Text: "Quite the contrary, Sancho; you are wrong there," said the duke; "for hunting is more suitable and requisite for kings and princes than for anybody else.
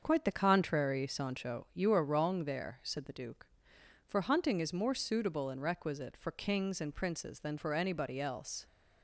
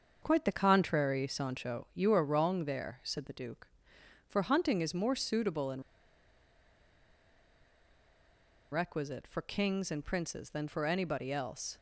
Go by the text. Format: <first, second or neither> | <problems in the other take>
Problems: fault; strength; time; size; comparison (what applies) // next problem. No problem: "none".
first | starts louder than the rest; until 1.2 s; 7 dB; also in the first // pauses between "and" and "requisite"; strong; at 5.8 s; 2.9 s long